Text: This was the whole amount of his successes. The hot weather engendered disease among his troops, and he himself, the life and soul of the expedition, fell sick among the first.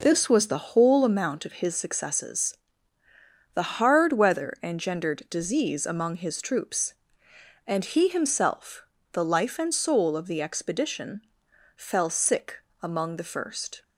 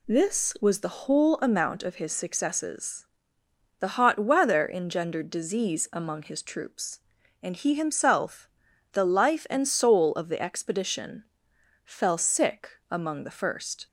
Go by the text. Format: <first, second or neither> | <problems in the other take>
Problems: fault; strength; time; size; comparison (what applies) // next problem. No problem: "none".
second | says "hard" for "hot"; at 3.7 s // pauses between "sick" and "among"; slight; at 12.6 s; 0.22 s long